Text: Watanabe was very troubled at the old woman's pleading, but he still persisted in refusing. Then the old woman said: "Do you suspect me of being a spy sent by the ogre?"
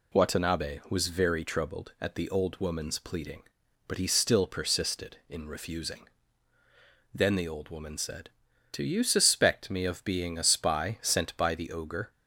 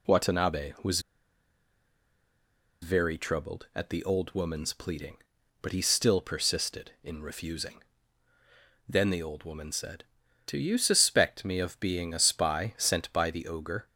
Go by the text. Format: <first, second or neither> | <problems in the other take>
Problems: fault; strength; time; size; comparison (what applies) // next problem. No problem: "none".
first | pauses between "was" and "very"; strong; at 0.9 s; 1.8 s long